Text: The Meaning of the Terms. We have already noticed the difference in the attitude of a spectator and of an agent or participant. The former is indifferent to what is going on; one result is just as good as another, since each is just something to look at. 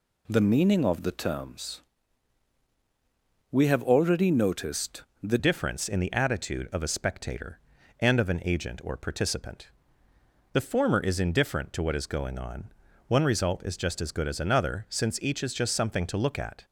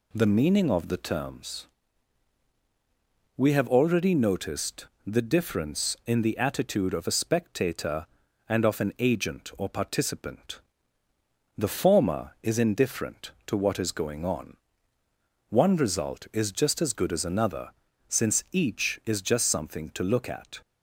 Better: second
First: pauses between "noticed" and "the"; slight; at 5.0 s; 0.18 s long // changes voice at "difference"; from 5.3 s on; 11.3 s long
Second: pauses between "noticed" and "the"; slight; at 4.8 s; 0.18 s long

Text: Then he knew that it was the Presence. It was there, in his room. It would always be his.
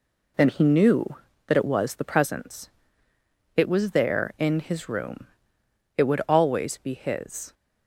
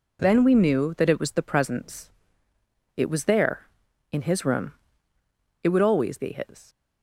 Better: first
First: none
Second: says "we" for "he"; at 0.4 s

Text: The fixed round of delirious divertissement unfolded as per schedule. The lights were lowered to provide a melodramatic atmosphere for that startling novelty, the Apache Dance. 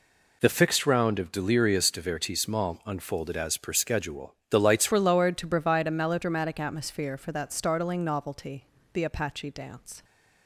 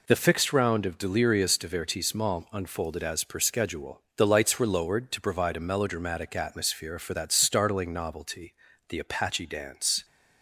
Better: second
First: changes voice at "were"; from 4.9 s on; 5.1 s long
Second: none

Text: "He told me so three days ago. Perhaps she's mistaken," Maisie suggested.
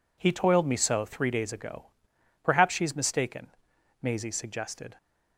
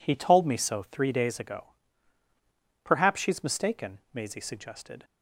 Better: second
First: says "toiled" for "told"; at 0.3 s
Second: none

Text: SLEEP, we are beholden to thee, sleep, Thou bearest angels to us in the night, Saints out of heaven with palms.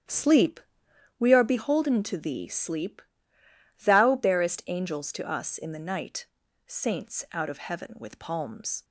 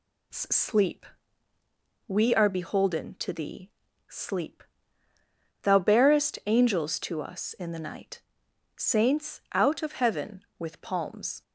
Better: second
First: starts louder than the rest; strong; until 1.2 s; 10.5 dB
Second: none

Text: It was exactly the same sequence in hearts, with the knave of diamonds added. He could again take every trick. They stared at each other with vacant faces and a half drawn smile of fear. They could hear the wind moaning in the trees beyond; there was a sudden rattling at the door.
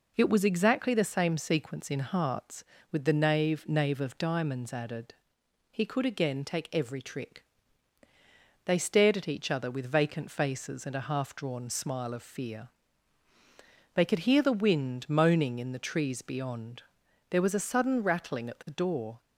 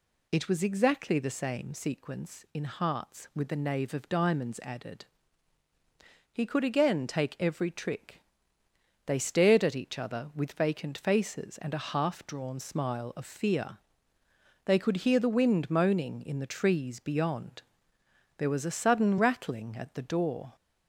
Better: second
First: says "knave" twice; at 3.6 s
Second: none

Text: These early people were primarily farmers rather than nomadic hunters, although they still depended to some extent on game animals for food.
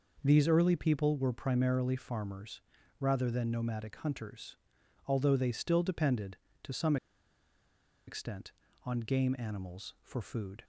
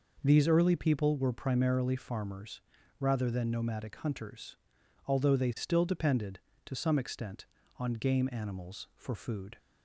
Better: second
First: pauses between "farmers" and "rather"; at 2.6 s; 0.40 s long // pauses between "some" and "extent"; at 6.9 s; 1.1 s long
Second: pauses between "farmers" and "rather"; at 2.5 s; 0.40 s long

